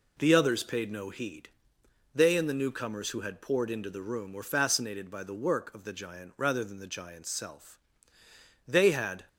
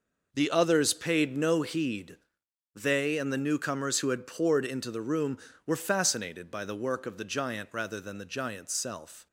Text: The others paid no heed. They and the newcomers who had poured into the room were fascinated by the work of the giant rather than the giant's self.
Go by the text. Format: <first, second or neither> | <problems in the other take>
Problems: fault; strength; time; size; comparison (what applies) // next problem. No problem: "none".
second | goes on to say "They had"; noticeable; from 8.6 s on; 0.62 s long